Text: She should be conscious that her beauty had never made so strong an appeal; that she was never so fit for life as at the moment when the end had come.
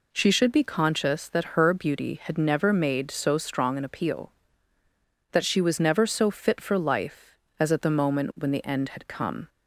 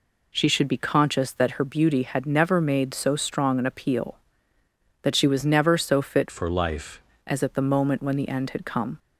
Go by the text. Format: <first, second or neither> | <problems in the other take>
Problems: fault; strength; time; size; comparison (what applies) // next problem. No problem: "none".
first | changes voice from "for" to "life"; from 6.2 to 7.0 s; 0.8 s long